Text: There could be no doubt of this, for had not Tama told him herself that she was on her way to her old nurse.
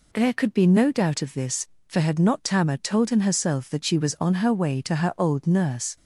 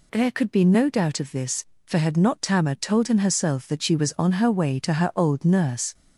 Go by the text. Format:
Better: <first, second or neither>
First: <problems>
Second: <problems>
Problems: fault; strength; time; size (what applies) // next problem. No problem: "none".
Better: first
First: none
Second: gets louder; slight; throughout; 2 dB